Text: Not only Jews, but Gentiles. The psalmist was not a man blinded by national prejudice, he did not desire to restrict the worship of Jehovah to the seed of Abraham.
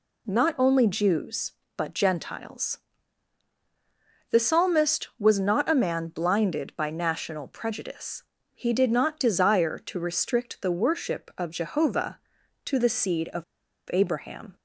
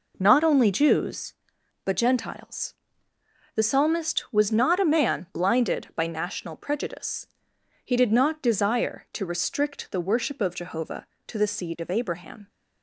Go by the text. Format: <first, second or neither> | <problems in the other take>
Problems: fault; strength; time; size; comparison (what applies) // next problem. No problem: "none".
second | pauses between "of" and "Abraham"; noticeable; at 13.4 s; 0.49 s long